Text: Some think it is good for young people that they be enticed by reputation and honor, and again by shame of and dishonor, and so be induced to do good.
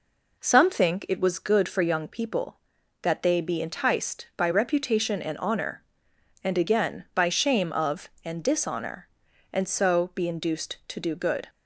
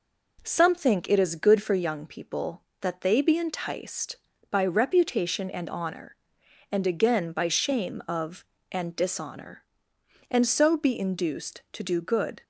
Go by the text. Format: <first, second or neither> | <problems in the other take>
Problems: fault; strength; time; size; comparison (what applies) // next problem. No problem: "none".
second | says "was" for "is"; at 1.1 s